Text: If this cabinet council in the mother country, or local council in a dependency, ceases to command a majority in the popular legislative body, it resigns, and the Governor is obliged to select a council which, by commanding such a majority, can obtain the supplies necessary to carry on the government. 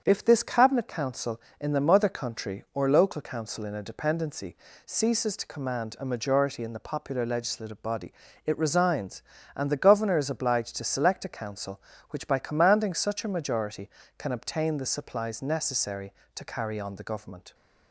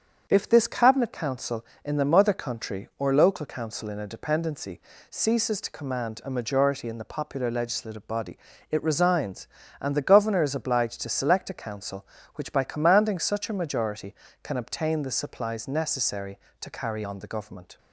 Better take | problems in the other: neither | starts louder than the rest; strong; the same in both

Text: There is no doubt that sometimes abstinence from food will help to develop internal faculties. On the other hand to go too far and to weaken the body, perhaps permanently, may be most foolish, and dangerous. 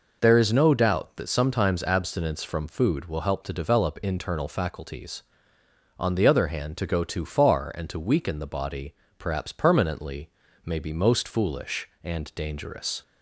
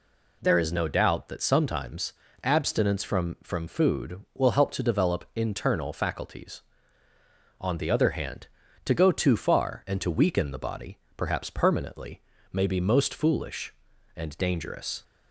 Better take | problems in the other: first | pauses between "sometimes" and "abstinence"; slight; at 2.1 s; 0.30 s long // says "from" twice; at 3.4 s

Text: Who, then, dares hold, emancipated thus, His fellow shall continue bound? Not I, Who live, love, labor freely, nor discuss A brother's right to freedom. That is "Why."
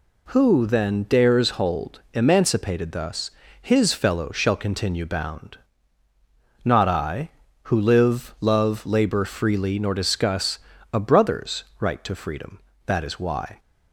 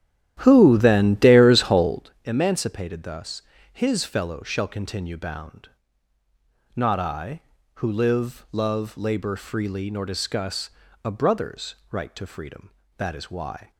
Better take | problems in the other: first | starts louder than the rest; strong; until 2.1 s; 11.5 dB // pauses between "discuss" and "A"; slight; at 10.7 s; 0.34 s long; slight in the first // pauses between "brother's" and "right"; slight; at 11.7 s; 0.16 s long; slight in the first

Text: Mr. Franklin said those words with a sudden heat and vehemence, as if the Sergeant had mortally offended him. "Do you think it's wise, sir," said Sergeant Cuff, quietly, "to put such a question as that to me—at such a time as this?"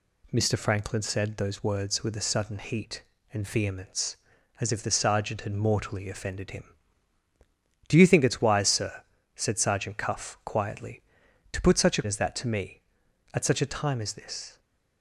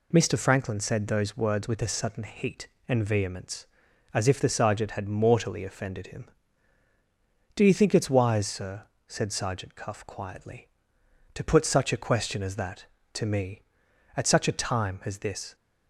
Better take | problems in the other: second | skips "question"; at 12.0 s

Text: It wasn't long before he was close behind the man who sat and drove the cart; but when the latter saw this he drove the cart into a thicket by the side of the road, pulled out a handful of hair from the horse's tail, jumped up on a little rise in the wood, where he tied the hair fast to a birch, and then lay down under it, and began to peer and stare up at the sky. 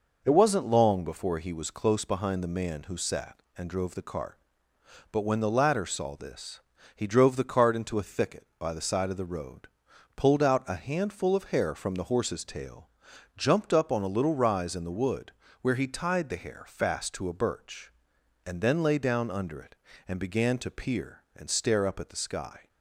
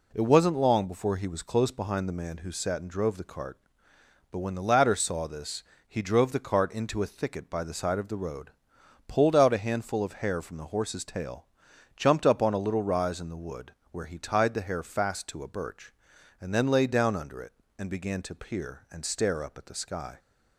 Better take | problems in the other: neither | pauses between "this" and "he"; slight; the same in both

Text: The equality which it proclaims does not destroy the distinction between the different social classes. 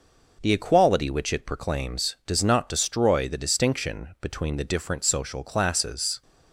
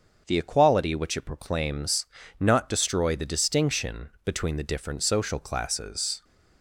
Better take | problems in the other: first | starts louder than the rest; until 1.2 s; 6.5 dB // skips "does"; at 2.2 s

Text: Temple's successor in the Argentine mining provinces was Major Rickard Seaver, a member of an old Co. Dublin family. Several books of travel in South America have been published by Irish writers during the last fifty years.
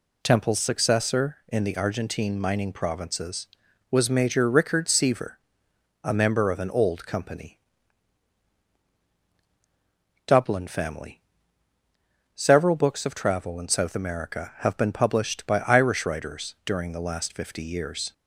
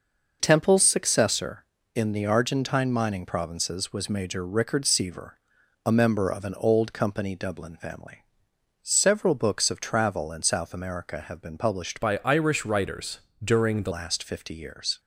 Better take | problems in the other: first | changes voice from "by" to "the"; from 12.0 to 13.9 s; 1.9 s long // pauses between "writers" and "during"; slight; at 13.2 s; 0.22 s long

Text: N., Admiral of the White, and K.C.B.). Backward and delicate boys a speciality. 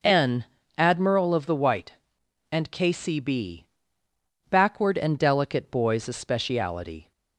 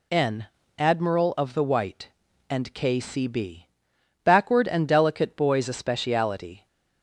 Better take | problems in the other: neither | none

